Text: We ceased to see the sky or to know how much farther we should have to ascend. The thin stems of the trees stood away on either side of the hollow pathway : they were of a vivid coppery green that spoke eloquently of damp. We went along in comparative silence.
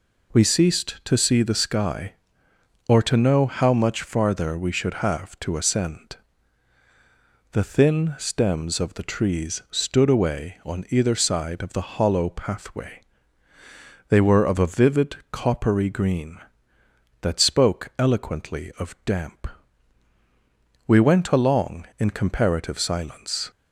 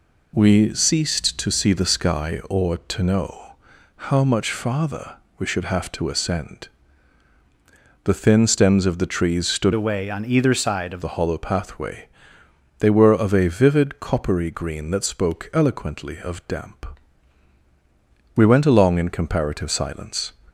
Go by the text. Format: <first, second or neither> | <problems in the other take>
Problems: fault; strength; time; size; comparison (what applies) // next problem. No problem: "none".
first | pauses between "know" and "how"; at 3.5 s; 0.42 s long // pauses between "farther" and "we"; slight; at 5.1 s; 0.24 s long // changes voice from "away" to "of"; from 9.7 to 11.0 s; 1.3 s long